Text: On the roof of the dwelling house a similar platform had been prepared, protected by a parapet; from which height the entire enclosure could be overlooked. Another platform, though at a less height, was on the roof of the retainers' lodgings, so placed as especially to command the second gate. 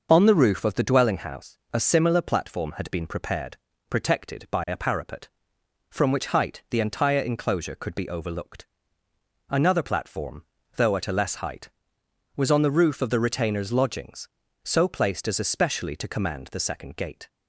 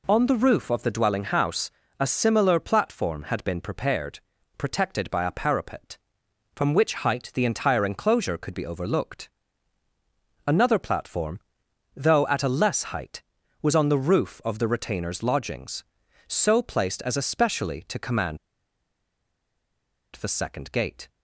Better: first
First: pauses between "house" and "a"; slight; at 1.5 s; 0.16 s long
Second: pauses between "house" and "a"; slight; at 1.7 s; 0.28 s long // pauses between "command" and "the"; strong; at 18.3 s; 1.7 s long

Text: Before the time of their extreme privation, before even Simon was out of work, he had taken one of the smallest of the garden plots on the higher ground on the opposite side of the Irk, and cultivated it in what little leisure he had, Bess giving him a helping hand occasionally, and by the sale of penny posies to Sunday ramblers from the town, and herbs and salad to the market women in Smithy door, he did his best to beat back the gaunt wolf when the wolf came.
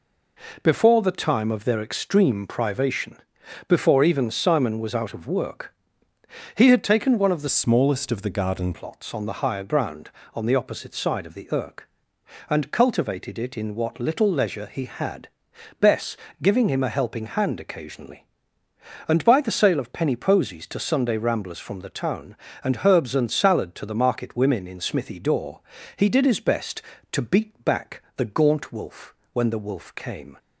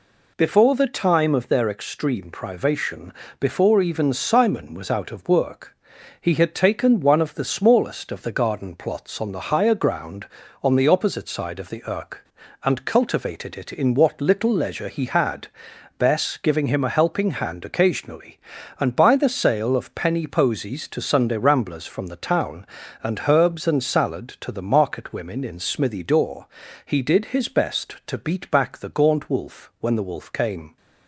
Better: second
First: changes voice from "smallest" to "garden"; from 7.4 to 8.7 s; 1.3 s long // pauses between "Bess" and "giving"; slight; at 16.1 s; 0.26 s long // pauses between "wolf" and "when"; slight; at 29.1 s; 0.18 s long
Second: none

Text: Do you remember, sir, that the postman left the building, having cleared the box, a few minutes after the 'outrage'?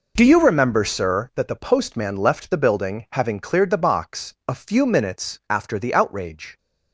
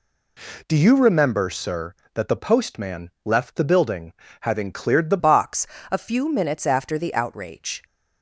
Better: first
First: none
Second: changes voice at "box"; from 5.1 s on; 2.7 s long

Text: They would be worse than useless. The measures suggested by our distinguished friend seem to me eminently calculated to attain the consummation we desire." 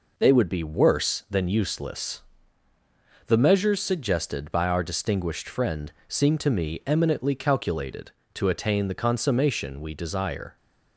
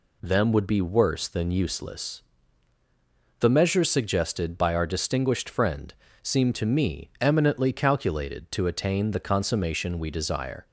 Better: first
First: pauses between "friend" and "seem"; slight; at 5.9 s; 0.16 s long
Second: says "Them" for "They"; at 0.2 s // pauses between "friend" and "seem"; slight; at 5.9 s; 0.28 s long

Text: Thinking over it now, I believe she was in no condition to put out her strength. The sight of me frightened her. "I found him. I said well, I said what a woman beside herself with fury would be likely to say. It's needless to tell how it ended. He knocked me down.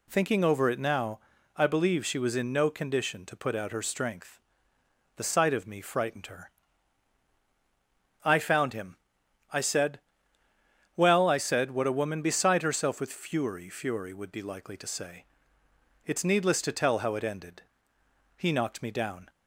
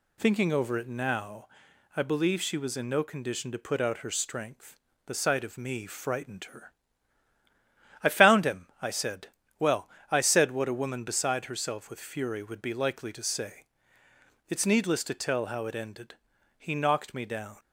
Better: second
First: pauses between "said" and "well"; noticeable; at 9.9 s; 0.98 s long // says "fury" twice; at 13.6 s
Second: pauses between "said" and "well"; slight; at 9.2 s; 0.32 s long

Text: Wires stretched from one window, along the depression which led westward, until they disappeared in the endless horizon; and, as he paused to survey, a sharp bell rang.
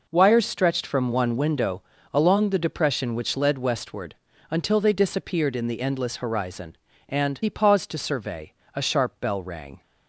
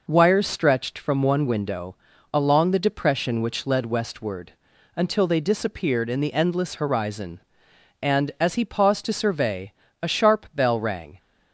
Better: second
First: skips "as"; at 7.4 s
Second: none

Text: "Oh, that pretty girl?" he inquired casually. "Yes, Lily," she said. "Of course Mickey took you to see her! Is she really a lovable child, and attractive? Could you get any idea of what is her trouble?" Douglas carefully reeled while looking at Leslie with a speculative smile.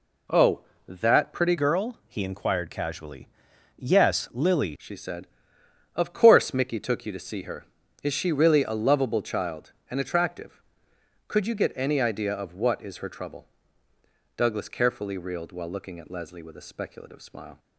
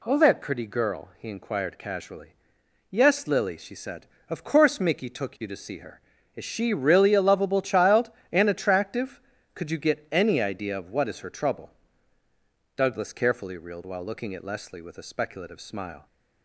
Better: second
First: changes voice from "girl" to "Lily"; from 1.5 to 4.7 s; 3.2 s long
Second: none

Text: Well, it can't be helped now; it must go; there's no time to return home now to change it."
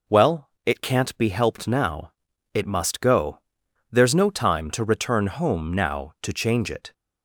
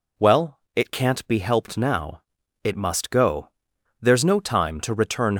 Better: first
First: none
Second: stops before "home now to change it"; at 5.3 s

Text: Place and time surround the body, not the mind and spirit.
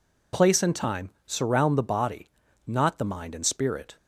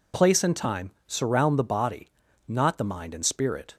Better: neither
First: pauses between "time" and "surround"; slight; at 1.1 s; 0.16 s long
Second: pauses between "time" and "surround"; slight; at 0.9 s; 0.16 s long

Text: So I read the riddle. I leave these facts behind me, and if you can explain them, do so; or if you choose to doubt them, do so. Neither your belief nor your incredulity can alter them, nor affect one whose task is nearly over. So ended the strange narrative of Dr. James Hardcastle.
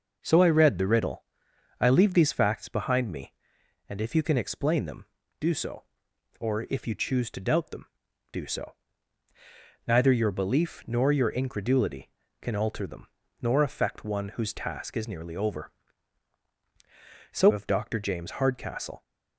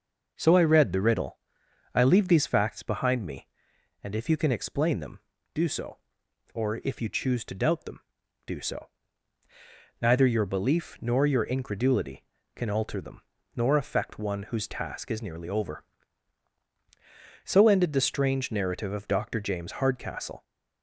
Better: second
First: skips "ended the strange narrative"; at 17.5 s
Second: none

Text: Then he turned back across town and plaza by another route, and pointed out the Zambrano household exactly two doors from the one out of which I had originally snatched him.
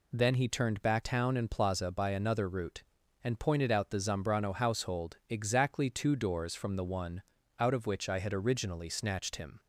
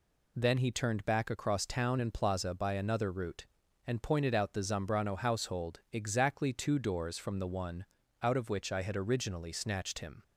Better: second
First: skips "across"; at 1.0 s // pauses between "one" and "out"; at 7.2 s; 0.38 s long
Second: pauses between "one" and "out"; at 7.8 s; 0.38 s long

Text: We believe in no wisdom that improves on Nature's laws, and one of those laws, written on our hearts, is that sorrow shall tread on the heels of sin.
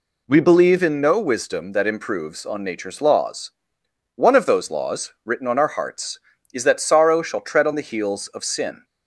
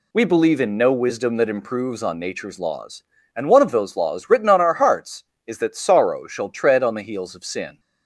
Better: second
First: skips "and"; at 3.8 s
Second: none

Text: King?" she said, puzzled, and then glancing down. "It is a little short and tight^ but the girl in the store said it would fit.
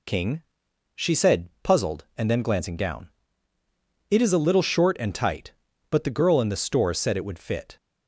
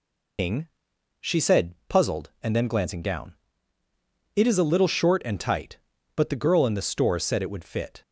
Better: first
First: none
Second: loses the start of "King"; at 0.3 s; 75 ms

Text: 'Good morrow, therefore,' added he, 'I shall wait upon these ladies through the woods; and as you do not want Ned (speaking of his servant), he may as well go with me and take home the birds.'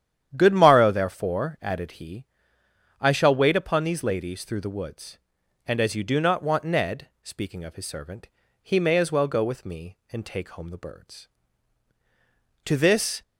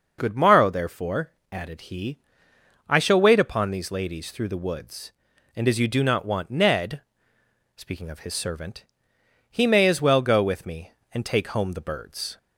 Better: second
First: starts louder than the rest; strong; until 1.3 s; 10 dB // goes on to say "To this"; from 12.6 s on; 0.58 s long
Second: none

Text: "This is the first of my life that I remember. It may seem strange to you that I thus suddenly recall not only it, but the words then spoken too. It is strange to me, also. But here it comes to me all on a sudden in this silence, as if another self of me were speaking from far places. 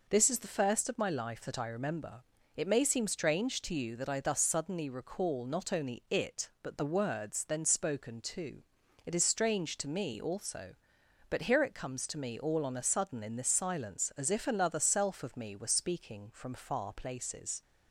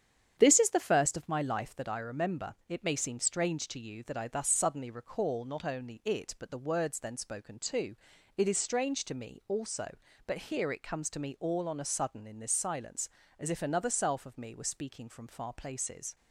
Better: first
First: none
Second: starts louder than the rest; strong; until 1.9 s; 9 dB

